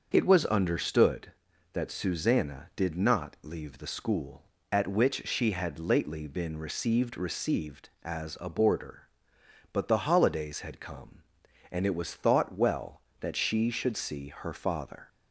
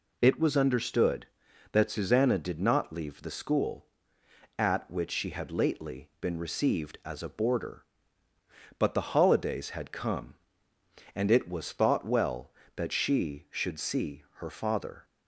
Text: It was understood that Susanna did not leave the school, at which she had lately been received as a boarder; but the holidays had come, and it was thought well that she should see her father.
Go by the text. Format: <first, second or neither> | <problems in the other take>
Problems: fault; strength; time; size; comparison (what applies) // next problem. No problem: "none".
second | starts louder than the rest; until 1.1 s; 6.5 dB // says "received" twice; at 7.1 s